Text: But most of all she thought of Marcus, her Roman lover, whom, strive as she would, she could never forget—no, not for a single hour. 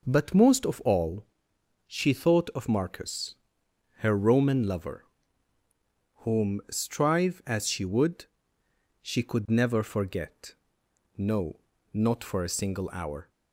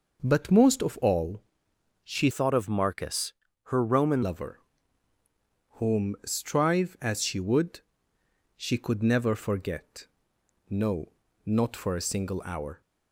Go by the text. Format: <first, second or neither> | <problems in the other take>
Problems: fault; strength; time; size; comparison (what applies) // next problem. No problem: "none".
first | pauses between "all" and "she"; noticeable; at 1.4 s; 0.62 s long; noticeable in the first // changes voice from "thought" to "Roman"; from 2.3 to 4.2 s; 1.9 s long